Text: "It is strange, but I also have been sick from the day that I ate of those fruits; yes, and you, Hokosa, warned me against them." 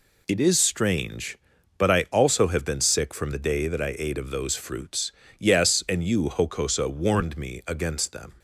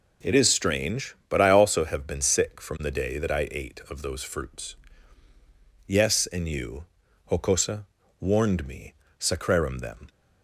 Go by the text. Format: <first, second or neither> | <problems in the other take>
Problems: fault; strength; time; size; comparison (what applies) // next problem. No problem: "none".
first | says "sacrarum" for "against"; at 9.1 s